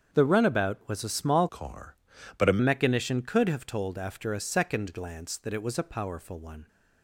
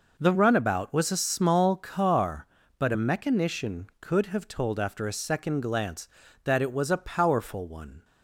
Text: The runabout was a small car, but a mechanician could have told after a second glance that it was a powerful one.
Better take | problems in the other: second | starts louder than the rest; strong; until 1.2 s; 7.5 dB // changes voice from "car" to "a"; from 1.4 to 2.5 s; 1.1 s long

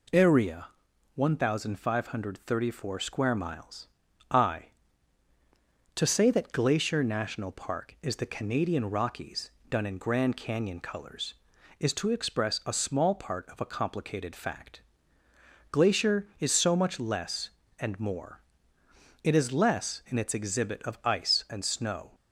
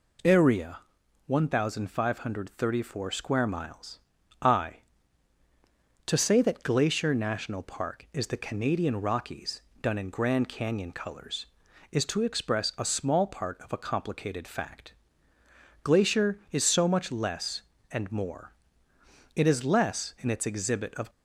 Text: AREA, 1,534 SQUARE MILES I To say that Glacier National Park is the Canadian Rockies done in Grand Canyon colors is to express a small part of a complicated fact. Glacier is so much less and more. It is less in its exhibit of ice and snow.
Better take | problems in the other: first | pauses between "MILES" and "I"; at 3.9 s; 0.41 s long; also in the first // pauses between "Rockies" and "done"; slight; at 9.6 s; 0.20 s long; slight in the first // stops before "ice and snow"; at 21.0 s

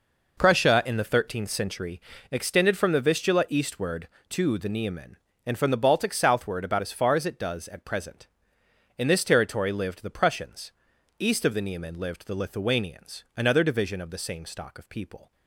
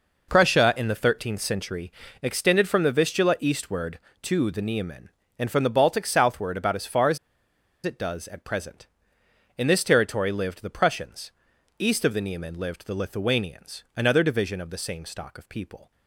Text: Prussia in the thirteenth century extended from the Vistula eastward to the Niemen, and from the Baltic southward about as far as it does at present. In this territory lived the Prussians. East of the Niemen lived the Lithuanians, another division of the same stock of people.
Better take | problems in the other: first | pauses between "century" and "extended"; slight; at 1.9 s; 0.30 s long; slight in the first // pauses between "as" and "it"; noticeable; at 7.1 s; 0.66 s long

